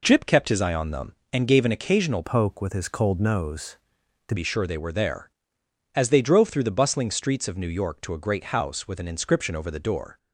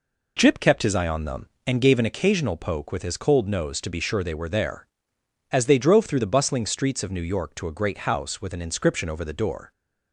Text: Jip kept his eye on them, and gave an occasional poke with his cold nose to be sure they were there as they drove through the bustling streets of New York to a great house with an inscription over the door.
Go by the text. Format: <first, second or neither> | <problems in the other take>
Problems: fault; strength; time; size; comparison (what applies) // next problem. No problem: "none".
second | changes voice from "poke" to "to"; from 2.2 to 4.3 s; 2.1 s long